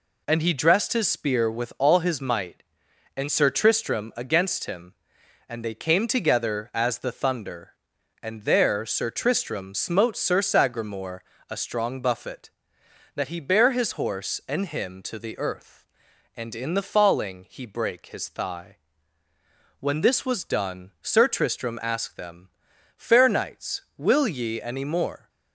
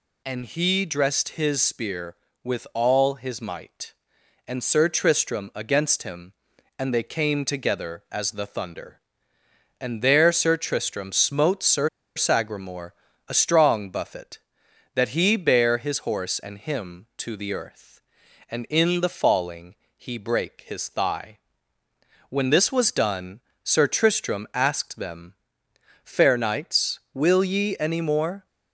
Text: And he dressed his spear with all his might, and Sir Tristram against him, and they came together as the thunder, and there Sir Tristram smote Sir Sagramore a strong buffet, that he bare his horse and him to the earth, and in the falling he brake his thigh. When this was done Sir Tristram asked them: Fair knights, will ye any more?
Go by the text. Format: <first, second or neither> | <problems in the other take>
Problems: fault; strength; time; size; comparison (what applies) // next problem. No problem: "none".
first | pauses between "Sir" and "Sagramore"; slight; at 11.8 s; 0.27 s long // pauses between "Sagramore" and "a"; slight; at 12.9 s; 0.34 s long; slight in the first // pauses between "falling" and "he"; slight; at 19.7 s; 0.22 s long // pauses between "done" and "Sir"; slight; at 23.4 s; 0.24 s long